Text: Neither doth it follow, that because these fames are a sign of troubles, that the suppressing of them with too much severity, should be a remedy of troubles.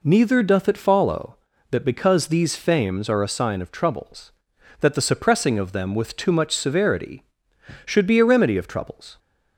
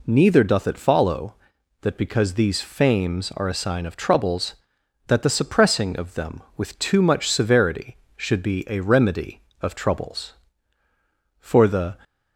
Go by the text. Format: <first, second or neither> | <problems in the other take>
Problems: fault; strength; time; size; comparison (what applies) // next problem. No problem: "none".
first | goes on to say "For the"; from 11.3 s on; 0.56 s long